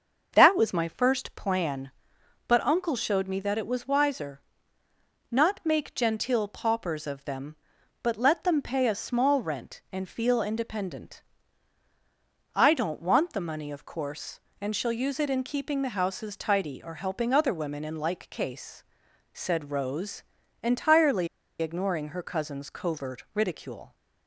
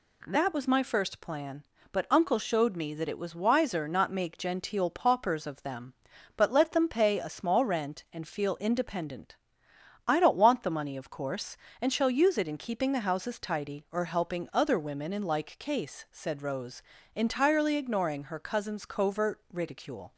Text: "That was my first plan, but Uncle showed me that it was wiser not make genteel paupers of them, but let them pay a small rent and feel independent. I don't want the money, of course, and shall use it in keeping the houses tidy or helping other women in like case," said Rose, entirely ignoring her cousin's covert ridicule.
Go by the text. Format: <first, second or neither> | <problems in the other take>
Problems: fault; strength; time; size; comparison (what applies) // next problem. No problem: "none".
second | starts louder than the rest; until 1.3 s; 6 dB // pauses between "wiser" and "not"; noticeable; at 4.3 s; 0.90 s long // pauses between "entirely" and "ignoring"; slight; at 21.2 s; 0.34 s long